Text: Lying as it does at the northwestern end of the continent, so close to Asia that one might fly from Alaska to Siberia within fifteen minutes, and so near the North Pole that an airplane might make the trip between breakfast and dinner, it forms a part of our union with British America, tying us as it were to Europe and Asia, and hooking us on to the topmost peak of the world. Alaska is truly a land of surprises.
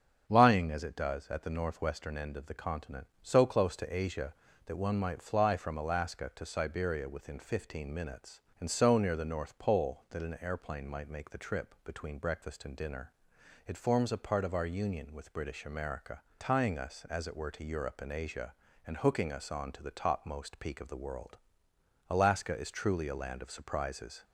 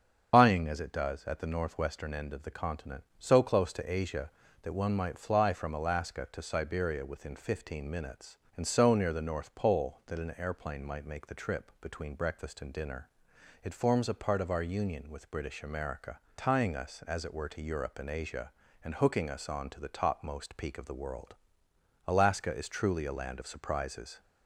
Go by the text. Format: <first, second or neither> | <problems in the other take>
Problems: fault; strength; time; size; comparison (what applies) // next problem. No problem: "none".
first | loses the start of "Lying"; at 0.3 s; 80 ms // starts louder than the rest; until 1.3 s; 7 dB; strong in the first